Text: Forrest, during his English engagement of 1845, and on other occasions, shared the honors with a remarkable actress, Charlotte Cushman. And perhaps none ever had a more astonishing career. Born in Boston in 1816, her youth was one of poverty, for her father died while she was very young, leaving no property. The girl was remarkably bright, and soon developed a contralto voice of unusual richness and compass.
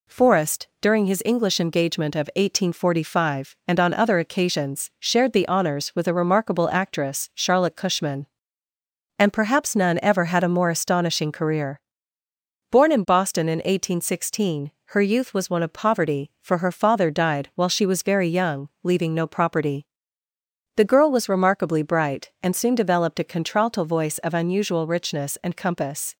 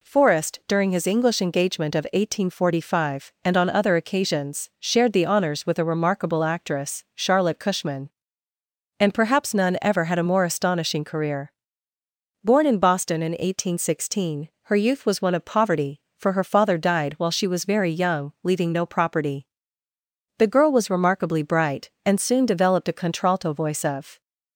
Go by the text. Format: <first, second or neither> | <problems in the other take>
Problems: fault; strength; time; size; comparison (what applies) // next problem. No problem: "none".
first | stops before "unusual richness and compass"; at 24.2 s